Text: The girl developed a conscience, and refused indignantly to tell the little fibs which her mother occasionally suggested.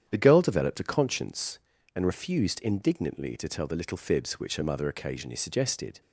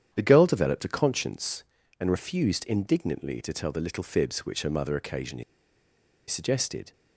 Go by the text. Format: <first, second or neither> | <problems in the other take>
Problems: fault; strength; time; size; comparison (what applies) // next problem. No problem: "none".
first | starts louder than the rest; strong; until 1.1 s; 9 dB; strong in the first // pauses between "occasionally" and "suggested"; noticeable; at 5.4 s; 0.84 s long